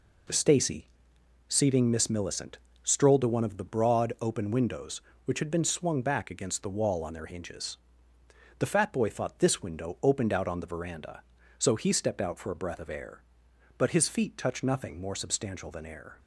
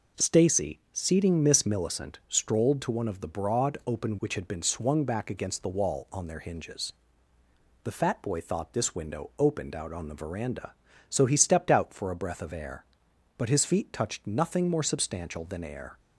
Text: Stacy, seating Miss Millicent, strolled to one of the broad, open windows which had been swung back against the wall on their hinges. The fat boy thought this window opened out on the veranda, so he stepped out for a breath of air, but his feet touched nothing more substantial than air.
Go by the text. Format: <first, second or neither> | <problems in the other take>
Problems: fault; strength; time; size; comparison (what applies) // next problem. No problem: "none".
first | skips "windows"; at 4.1 s